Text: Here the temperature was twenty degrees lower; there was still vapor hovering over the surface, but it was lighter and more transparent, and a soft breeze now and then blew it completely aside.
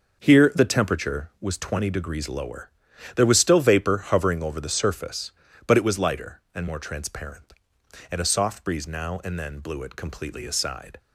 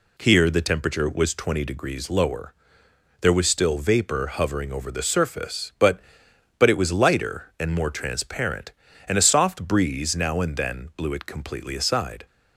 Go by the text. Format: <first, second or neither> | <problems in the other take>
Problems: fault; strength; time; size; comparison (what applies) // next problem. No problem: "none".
first | says "but" twice; at 6.5 s